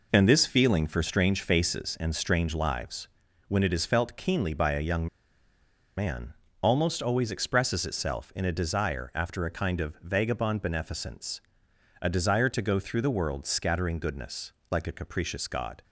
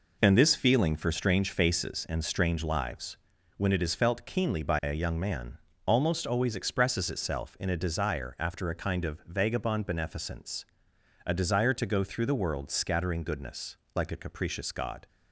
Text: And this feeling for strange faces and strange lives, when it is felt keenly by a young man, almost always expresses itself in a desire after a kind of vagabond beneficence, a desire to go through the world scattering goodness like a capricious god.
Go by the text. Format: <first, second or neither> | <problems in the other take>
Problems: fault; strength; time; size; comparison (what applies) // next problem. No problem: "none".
second | pauses between "young" and "man"; noticeable; at 5.0 s; 0.90 s long // pauses between "goodness" and "like"; slight; at 14.5 s; 0.20 s long; slight in the second